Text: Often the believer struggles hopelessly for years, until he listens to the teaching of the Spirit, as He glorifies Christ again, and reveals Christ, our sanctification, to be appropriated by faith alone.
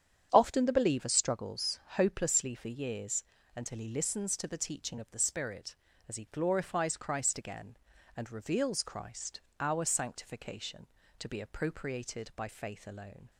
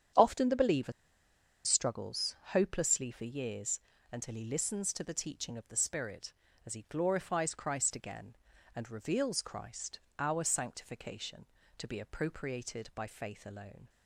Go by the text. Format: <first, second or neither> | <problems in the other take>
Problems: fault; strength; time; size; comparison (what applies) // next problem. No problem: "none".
first | starts louder than the rest; strong; until 1.8 s; 9 dB; strong in the first // pauses between "believer" and "struggles"; noticeable; at 0.9 s; 0.72 s long // pauses between "struggles" and "hopelessly"; slight; at 2.3 s; 0.16 s long; slight in the first